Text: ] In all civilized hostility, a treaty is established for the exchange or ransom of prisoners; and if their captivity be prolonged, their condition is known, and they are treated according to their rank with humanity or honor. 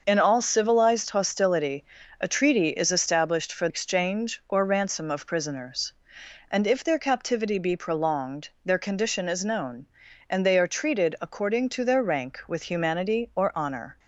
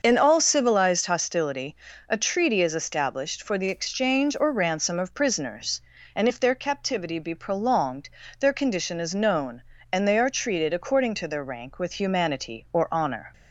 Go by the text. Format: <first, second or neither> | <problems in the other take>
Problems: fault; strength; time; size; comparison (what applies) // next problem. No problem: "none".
second | starts louder than the rest; until 1.0 s; 6.5 dB; also in the second // skips "the"; at 3.6 s